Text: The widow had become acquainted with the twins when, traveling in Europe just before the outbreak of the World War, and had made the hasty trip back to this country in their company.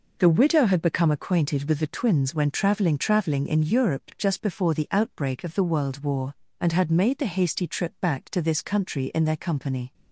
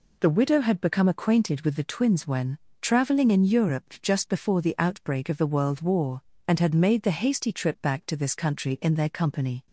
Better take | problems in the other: second | says "traveling" twice; at 2.9 s

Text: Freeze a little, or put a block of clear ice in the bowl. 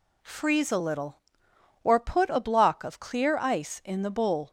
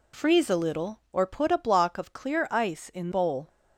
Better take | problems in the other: first | skips "the"; at 3.1 s

